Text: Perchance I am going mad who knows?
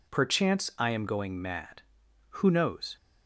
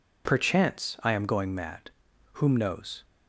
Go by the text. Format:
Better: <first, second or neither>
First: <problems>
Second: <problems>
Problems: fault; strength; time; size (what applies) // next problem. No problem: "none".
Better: first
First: none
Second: says "whom" for "who"; at 2.3 s